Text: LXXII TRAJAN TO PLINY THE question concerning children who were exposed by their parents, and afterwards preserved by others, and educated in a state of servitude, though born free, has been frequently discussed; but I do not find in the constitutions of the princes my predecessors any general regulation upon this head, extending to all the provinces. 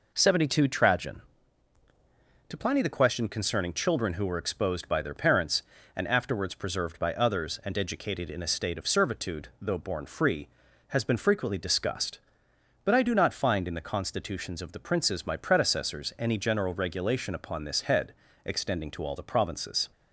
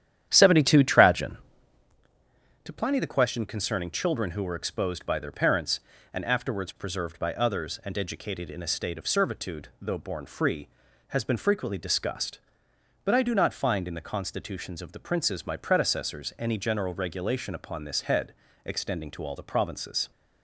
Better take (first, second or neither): first